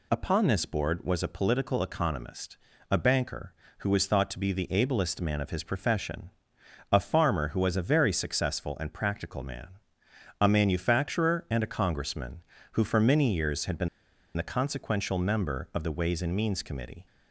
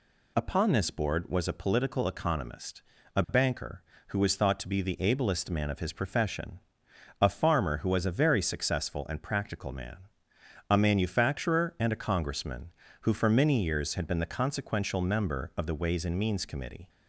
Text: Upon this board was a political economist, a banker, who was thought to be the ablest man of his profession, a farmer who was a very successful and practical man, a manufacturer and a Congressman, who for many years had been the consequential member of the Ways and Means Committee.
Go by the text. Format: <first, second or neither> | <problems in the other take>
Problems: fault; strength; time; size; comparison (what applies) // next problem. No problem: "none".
second | pauses between "been" and "the"; noticeable; at 13.8 s; 0.47 s long